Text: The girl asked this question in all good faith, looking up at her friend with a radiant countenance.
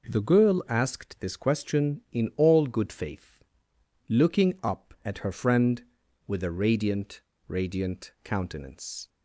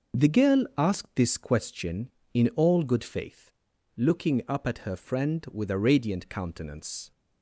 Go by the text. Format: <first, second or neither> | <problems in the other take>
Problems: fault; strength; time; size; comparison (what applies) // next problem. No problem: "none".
second | says "radiant" twice; at 7.4 s